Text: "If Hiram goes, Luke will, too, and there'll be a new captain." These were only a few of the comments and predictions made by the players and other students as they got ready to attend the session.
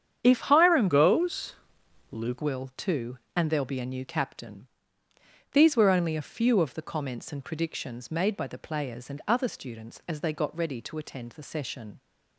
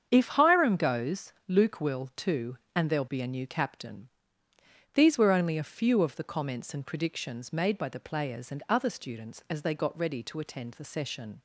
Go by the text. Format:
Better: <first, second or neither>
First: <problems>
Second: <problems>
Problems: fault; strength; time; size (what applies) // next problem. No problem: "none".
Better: second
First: starts louder than the rest; strong; until 1.2 s; 8.5 dB // changes voice from "goes" to "Luke"; from 0.8 to 2.4 s; 1.6 s long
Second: starts louder than the rest; strong; until 1.1 s; 7.5 dB